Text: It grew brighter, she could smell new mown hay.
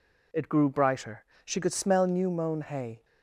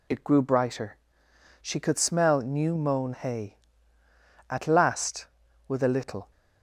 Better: first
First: none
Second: goes on to say "At last with a little"; strong; from 4.4 s on; 1.8 s long

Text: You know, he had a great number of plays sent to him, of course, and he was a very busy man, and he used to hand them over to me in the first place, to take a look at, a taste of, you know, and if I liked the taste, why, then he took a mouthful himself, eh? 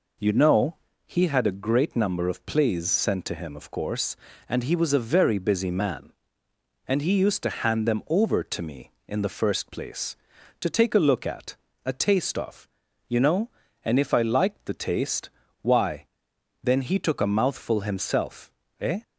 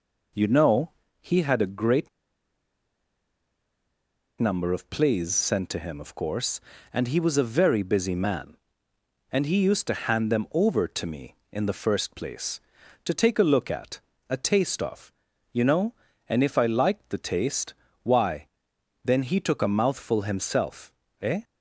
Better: first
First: none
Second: pauses between "great" and "number"; strong; at 2.0 s; 2.3 s long

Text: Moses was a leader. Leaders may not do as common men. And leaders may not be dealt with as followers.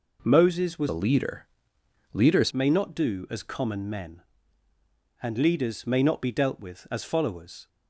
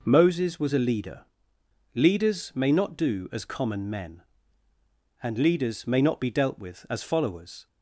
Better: second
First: changes voice from "a" to "Leaders"; from 0.8 to 2.5 s; 1.7 s long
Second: none

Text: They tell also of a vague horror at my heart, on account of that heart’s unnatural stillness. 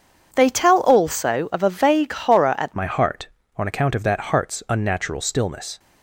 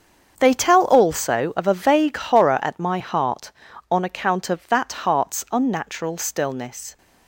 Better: second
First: starts louder than the rest; strong; until 1.3 s; 7.5 dB // changes voice at "my"; from 2.7 s on; 3.0 s long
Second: starts louder than the rest; strong; until 1.3 s; 7 dB

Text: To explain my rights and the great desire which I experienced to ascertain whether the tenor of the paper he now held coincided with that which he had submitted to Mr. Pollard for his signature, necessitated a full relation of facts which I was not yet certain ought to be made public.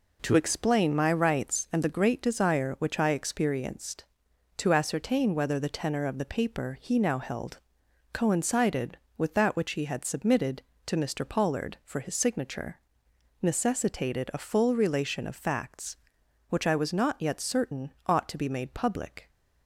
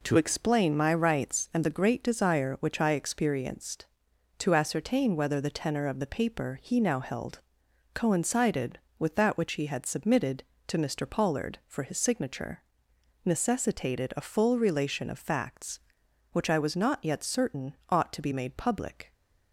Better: neither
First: pauses between "held" and "coincided"; noticeable; at 7.5 s; 0.54 s long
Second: pauses between "held" and "coincided"; noticeable; at 7.3 s; 0.54 s long

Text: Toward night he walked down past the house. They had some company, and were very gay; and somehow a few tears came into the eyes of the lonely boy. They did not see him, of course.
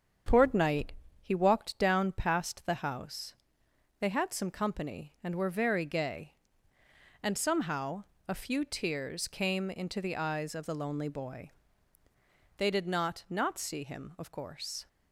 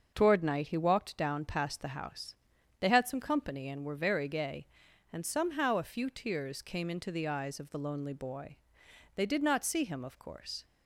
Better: second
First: starts louder than the rest; strong; until 1.5 s; 7.5 dB // pauses between "night" and "he"; slight; at 0.9 s; 0.30 s long // pauses between "somehow" and "a"; slight; at 8.0 s; 0.24 s long // says "not" twice; at 13.2 s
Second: starts louder than the rest; until 1.1 s; 6.5 dB

